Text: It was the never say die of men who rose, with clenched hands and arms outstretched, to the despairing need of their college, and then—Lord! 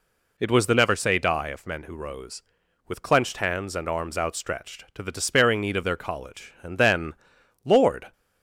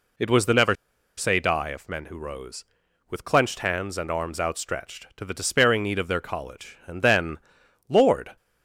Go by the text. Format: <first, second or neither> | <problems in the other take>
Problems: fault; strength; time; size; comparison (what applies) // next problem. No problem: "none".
first | pauses between "never" and "say"; at 0.7 s; 0.43 s long